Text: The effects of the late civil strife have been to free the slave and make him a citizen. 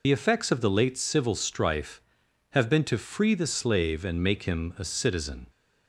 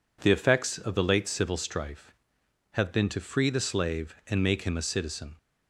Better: second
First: loses the start of "The"; at 0.0 s; 50 ms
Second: none

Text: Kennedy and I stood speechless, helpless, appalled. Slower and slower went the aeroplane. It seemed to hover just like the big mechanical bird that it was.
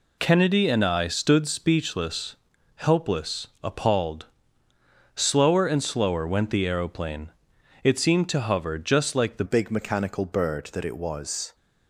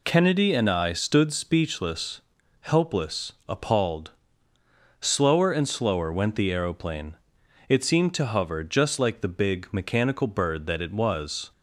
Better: second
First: changes voice at "big"; from 9.4 s on; 2.1 s long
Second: none

